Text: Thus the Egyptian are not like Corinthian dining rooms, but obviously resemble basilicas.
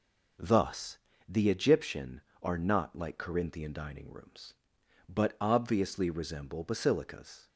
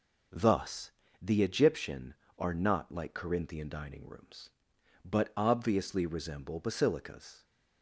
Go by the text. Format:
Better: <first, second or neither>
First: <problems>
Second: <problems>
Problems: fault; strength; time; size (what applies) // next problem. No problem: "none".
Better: neither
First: pauses between "Thus" and "the"; slight; at 0.9 s; 0.32 s long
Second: pauses between "Thus" and "the"; slight; at 0.8 s; 0.32 s long